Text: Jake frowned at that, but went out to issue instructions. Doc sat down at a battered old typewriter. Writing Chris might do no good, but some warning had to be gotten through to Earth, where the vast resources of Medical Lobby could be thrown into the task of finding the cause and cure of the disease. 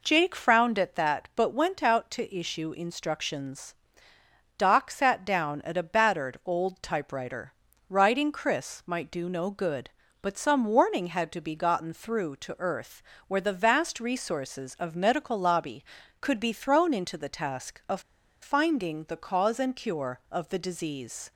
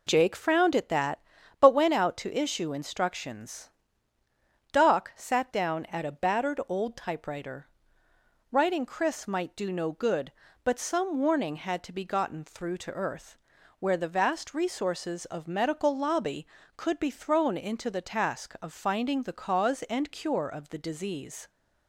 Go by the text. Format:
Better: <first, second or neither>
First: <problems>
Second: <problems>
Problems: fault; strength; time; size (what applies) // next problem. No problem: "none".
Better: second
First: pauses between "of" and "finding"; at 18.0 s; 0.41 s long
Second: none